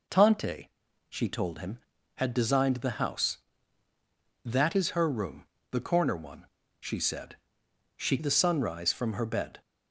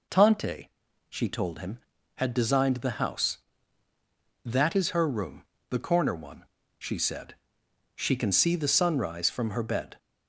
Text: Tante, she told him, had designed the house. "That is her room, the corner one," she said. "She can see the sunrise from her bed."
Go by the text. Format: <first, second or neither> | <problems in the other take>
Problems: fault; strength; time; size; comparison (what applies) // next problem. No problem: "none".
second | skips "can see"; at 8.1 s